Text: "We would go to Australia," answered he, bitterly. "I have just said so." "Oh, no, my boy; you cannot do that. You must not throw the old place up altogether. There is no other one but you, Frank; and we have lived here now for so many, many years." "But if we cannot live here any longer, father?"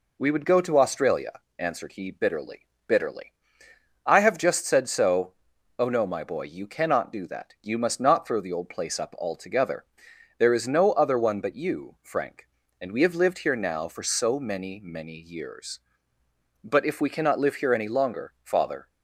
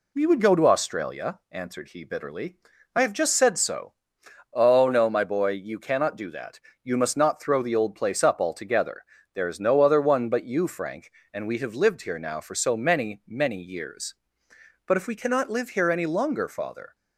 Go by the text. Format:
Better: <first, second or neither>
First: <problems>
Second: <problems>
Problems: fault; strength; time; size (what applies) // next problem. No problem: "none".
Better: second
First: says "bitterly" twice; at 2.8 s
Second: none